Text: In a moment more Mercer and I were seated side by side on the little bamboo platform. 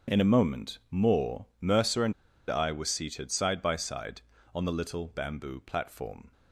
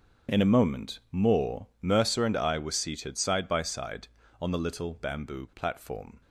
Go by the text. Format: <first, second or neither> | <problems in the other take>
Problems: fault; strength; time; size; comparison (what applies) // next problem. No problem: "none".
second | starts louder than the rest; strong; until 1.1 s; 7.5 dB; strong in the second // pauses between "more" and "Mercer"; slight; at 1.4 s; 0.16 s long; slight in the second // pauses between "and" and "I"; at 2.1 s; 0.36 s long